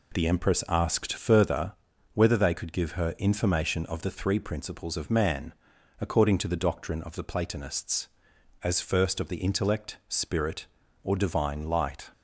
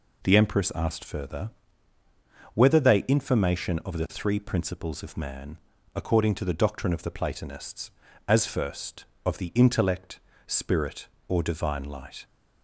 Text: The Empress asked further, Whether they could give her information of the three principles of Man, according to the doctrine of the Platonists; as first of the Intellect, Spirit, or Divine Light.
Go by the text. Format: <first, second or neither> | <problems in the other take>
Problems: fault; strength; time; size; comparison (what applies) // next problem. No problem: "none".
first | skips "could give her"; at 3.0 s